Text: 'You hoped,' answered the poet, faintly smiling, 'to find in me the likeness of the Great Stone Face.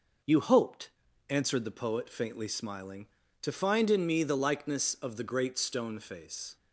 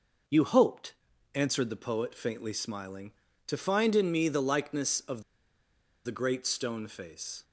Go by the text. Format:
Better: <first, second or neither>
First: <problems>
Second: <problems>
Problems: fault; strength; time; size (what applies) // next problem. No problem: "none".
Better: first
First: none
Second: pauses between "of" and "the"; noticeable; at 5.2 s; 0.82 s long